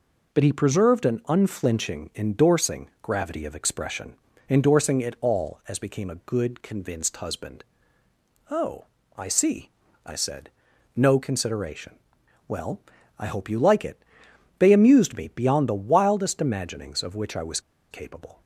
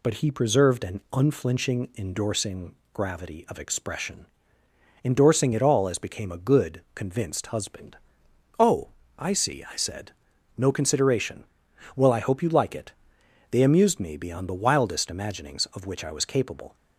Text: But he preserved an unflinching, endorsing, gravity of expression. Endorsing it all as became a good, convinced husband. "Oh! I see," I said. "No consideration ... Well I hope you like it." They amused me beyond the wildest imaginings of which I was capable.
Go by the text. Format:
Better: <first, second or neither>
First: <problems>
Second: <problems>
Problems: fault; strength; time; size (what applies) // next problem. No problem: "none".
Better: second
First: pauses between "Well" and "I"; at 12.7 s; 0.38 s long // pauses between "was" and "capable"; slight; at 17.5 s; 0.31 s long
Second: none